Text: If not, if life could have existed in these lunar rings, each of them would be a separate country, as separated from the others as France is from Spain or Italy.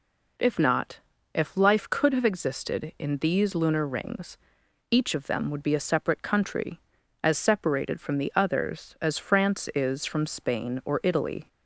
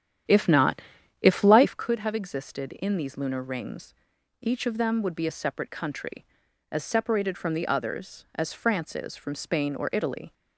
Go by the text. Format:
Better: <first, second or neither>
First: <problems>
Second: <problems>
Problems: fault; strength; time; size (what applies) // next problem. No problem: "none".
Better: first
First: none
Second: starts louder than the rest; strong; until 1.9 s; 10 dB